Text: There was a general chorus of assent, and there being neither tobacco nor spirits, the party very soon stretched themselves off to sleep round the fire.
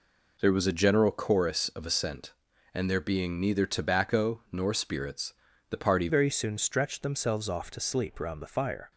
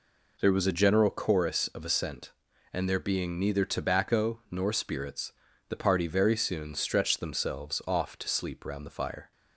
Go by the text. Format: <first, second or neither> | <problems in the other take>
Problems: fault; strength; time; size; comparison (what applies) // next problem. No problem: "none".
second | changes voice at "very"; from 6.0 s on; 2.9 s long